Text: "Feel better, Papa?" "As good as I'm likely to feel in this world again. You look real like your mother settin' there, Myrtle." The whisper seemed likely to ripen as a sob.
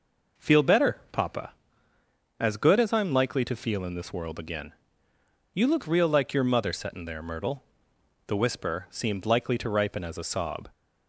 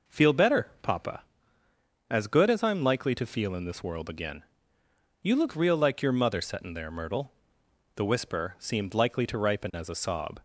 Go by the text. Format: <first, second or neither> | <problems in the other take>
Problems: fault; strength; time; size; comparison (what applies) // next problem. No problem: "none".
neither | none